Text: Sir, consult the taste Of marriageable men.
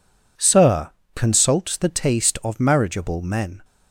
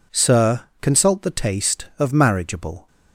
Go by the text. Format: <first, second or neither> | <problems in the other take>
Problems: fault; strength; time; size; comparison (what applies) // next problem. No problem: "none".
first | stops before "men"; at 2.8 s